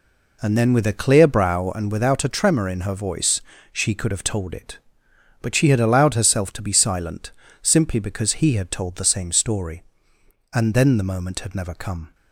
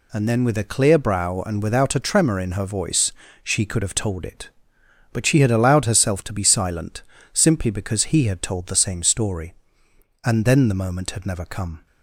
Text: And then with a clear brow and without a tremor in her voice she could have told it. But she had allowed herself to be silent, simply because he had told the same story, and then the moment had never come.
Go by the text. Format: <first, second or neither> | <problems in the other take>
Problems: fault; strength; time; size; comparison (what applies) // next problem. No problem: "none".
second | starts louder than the rest; slight; until 1.9 s; 3 dB // pauses between "voice" and "she"; slight; at 3.4 s; 0.32 s long; slight in the second